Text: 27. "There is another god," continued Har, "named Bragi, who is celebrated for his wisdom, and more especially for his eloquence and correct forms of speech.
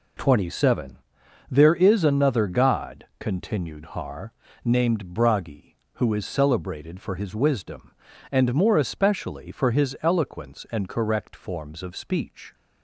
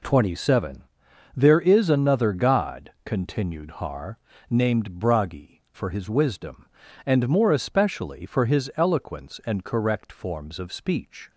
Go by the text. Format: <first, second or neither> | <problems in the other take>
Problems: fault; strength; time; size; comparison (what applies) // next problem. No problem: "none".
first | skips "who is celebrated"; at 5.6 s